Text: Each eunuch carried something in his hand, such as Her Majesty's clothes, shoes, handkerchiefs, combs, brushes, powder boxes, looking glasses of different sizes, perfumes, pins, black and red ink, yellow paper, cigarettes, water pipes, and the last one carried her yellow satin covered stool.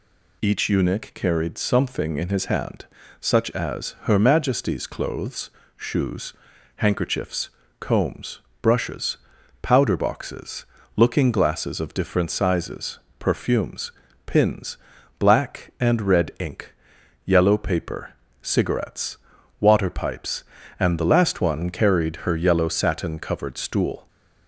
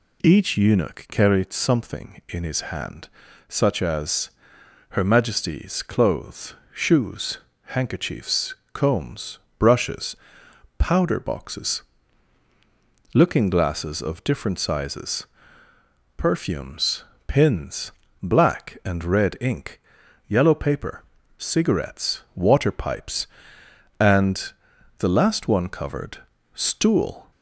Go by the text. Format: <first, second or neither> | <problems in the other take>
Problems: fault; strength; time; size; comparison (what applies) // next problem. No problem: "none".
first | pauses between "as" and "Her"; noticeable; at 4.2 s; 0.60 s long // pauses between "and" and "the"; noticeable; at 24.5 s; 0.46 s long // skips "carried her yellow satin"; at 25.6 s // pauses between "covered" and "stool"; slight; at 26.1 s; 0.34 s long